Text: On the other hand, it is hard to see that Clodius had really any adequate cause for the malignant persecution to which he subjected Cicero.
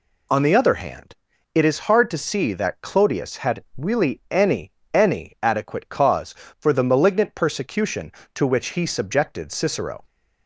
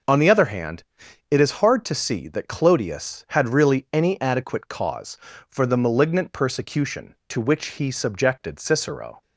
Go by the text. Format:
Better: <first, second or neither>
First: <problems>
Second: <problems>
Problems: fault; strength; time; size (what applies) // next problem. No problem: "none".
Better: second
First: says "any" twice; at 4.9 s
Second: none